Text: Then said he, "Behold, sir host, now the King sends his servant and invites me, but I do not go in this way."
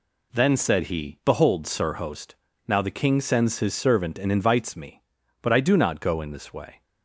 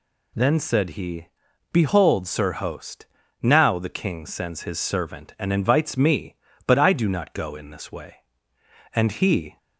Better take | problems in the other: first | goes on to say "And he"; noticeable; from 8.9 s on; 0.62 s long

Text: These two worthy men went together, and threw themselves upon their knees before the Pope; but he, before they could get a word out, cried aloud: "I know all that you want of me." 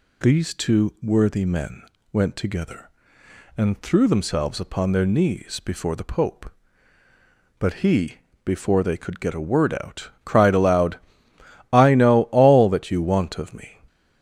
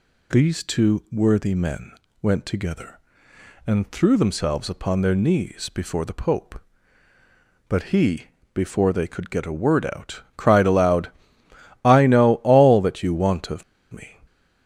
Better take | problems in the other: first | pauses between "men" and "went"; slight; at 1.9 s; 0.30 s long; slight in the first // pauses between "of" and "me"; slight; at 13.6 s; 0.28 s long

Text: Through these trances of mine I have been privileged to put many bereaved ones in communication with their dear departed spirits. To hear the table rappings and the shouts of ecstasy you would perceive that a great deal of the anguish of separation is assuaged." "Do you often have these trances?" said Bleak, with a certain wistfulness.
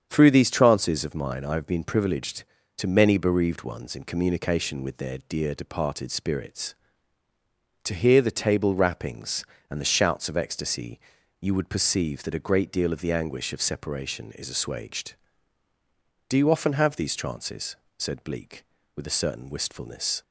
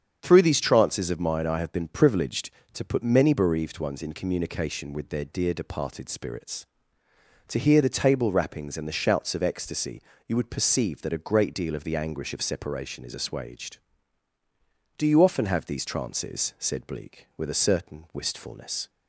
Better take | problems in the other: second | starts louder than the rest; strong; until 1.1 s; 8 dB; strong in the second // skips "put"; at 2.8 s // pauses between "ecstasy" and "you"; at 10.9 s; 0.40 s long; slight in the second

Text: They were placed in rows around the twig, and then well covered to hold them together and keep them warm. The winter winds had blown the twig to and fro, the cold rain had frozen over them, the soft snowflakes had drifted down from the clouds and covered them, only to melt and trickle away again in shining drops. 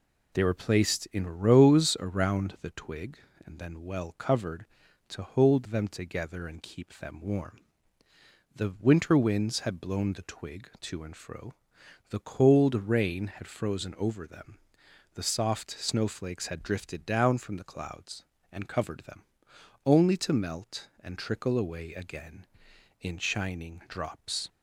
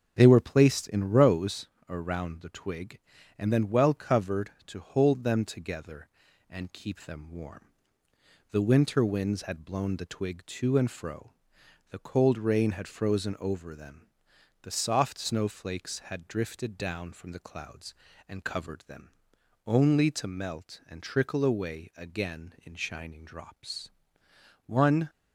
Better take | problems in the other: first | starts louder than the rest; until 1.1 s; 6.5 dB // pauses between "rows" and "around"; slight; at 1.6 s; 0.20 s long // goes on to say "One"; slight; from 24.6 s on; 0.44 s long

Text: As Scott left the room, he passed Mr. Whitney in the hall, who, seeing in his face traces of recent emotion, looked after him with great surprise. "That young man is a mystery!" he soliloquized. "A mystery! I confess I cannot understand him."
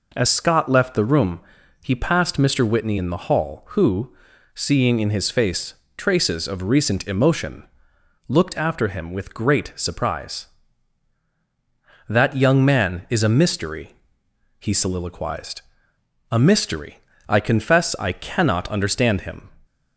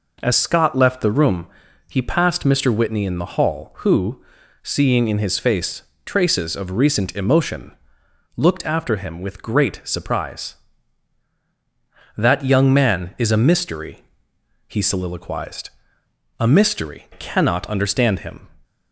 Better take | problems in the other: first | pauses between "face" and "traces"; slight; at 5.8 s; 0.22 s long; slight in the first // skips "I confess I"; at 17.0 s

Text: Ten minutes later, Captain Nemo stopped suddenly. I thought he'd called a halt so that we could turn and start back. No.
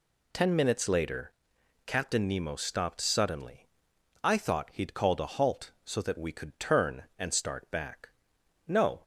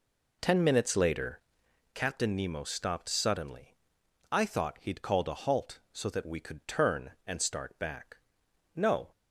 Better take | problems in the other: first | starts louder than the rest; until 1.8 s; 3.5 dB

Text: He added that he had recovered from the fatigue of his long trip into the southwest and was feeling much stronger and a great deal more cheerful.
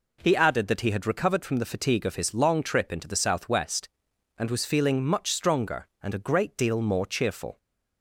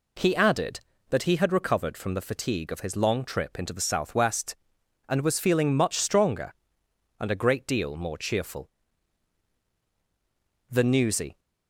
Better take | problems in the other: first | goes on to say "The newsy"; noticeable; from 10.6 s on; 0.70 s long

